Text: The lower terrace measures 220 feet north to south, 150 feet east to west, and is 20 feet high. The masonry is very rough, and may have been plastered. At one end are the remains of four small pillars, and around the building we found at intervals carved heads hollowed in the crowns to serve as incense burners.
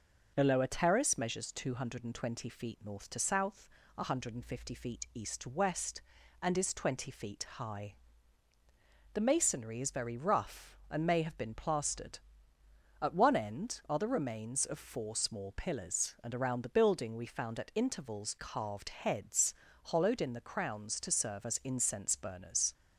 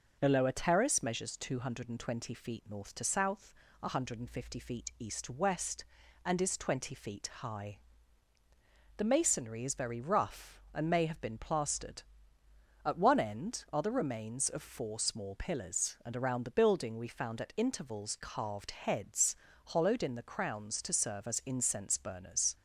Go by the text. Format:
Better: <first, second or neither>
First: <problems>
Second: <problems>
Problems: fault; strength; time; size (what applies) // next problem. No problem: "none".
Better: neither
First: pauses between "heads" and "hollowed"; slight; at 19.5 s; 0.32 s long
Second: pauses between "heads" and "hollowed"; slight; at 19.3 s; 0.32 s long